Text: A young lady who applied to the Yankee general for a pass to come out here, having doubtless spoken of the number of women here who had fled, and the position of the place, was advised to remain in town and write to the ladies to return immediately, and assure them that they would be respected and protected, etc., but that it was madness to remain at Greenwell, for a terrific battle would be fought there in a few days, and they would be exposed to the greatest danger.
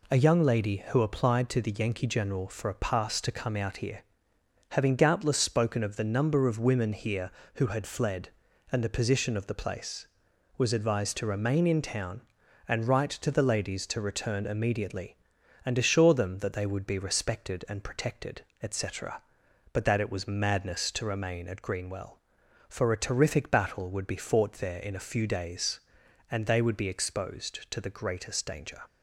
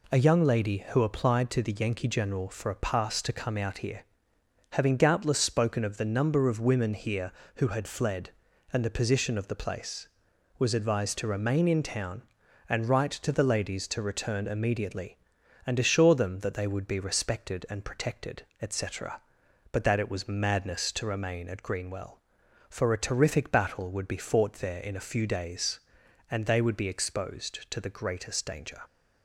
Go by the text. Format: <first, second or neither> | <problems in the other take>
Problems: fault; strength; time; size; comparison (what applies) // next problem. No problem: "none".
neither | none